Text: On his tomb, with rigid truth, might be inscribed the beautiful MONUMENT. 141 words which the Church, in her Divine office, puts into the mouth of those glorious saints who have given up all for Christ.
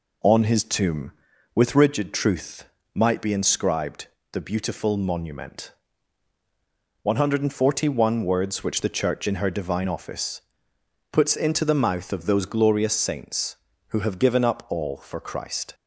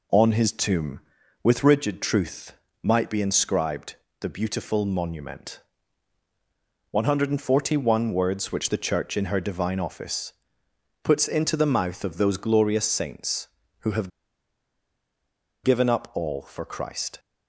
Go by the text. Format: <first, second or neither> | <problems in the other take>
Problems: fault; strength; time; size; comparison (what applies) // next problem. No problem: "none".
first | pauses between "inscribed" and "the"; slight; at 3.9 s; 0.28 s long; slight in the first // pauses between "have" and "given"; strong; at 14.0 s; 1.5 s long